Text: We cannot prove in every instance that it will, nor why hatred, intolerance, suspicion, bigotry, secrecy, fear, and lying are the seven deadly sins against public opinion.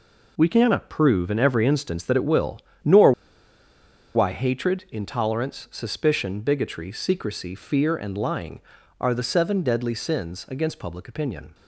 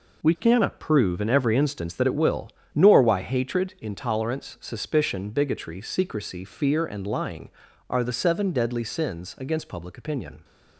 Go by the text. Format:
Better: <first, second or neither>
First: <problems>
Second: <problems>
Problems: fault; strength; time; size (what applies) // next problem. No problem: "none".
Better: second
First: pauses between "nor" and "why"; at 3.1 s; 1.0 s long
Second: none